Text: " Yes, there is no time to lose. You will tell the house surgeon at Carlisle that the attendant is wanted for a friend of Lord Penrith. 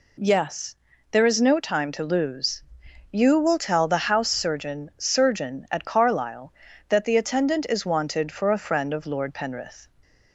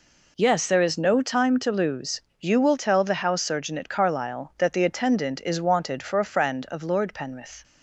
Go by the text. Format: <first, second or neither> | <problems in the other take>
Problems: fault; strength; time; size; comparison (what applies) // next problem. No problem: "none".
second | says "surgeon" twice; at 4.9 s